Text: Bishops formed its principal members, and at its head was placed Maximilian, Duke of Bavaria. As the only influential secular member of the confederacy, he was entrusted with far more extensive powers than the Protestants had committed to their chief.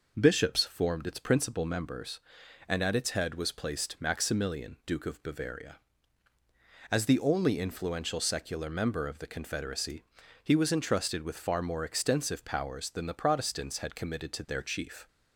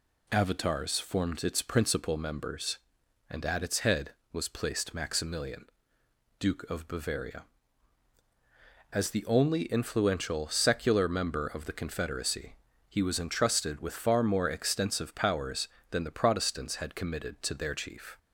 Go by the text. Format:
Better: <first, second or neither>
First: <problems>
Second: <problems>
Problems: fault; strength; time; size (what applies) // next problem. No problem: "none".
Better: first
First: none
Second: says "Avatars" for "Bishops"; at 0.2 s